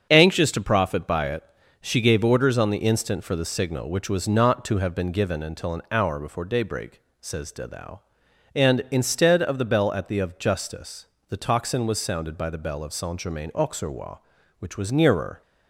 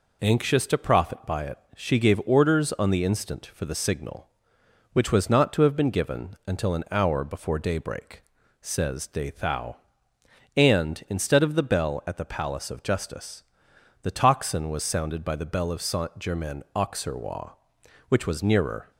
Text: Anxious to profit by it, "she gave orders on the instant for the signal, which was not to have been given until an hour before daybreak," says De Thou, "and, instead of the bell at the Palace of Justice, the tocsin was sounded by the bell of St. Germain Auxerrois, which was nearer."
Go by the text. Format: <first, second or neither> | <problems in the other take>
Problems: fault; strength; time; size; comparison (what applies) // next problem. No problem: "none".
second | starts louder than the rest; until 1.1 s; 7 dB // skips "Palace"; at 10.1 s